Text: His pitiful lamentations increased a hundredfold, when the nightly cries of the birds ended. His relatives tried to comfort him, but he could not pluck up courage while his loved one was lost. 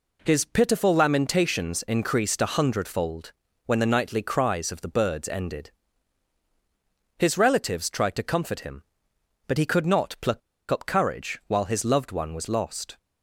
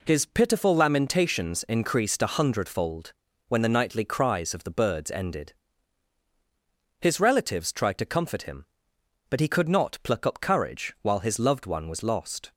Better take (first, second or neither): second